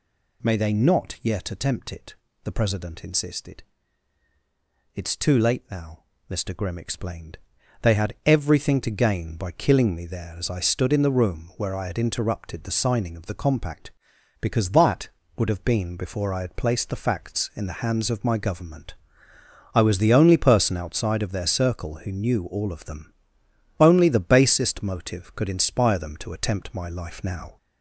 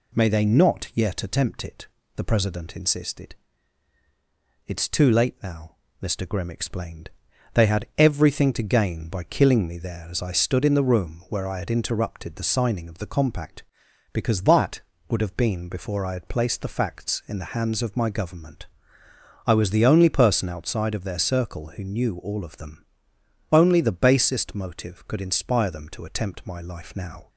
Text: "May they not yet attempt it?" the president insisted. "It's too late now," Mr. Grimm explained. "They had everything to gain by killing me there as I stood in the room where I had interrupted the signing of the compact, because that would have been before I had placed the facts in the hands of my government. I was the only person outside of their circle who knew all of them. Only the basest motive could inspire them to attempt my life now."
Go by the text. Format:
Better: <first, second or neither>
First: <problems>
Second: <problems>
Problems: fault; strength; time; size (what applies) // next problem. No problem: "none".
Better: second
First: gets louder; slight; throughout; 2.5 dB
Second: none